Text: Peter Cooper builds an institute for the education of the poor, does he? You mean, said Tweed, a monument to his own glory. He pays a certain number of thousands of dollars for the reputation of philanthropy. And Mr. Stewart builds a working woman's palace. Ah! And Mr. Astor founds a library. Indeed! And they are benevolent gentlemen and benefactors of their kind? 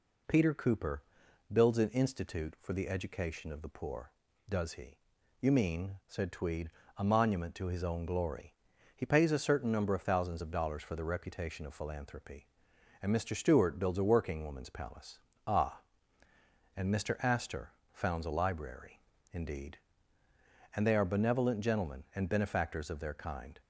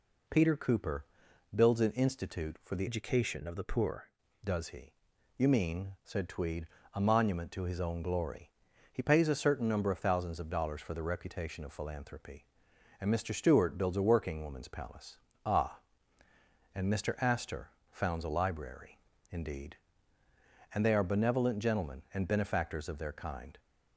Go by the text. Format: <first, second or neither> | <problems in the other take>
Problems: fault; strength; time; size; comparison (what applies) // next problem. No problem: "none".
first | pauses between "Cooper" and "builds"; noticeable; at 1.0 s; 0.50 s long; noticeable in the first // changes voice from "education" to "poor"; from 2.8 to 4.0 s; 1.2 s long // pauses between "Astor" and "founds"; slight; at 17.6 s; 0.20 s long; slight in the first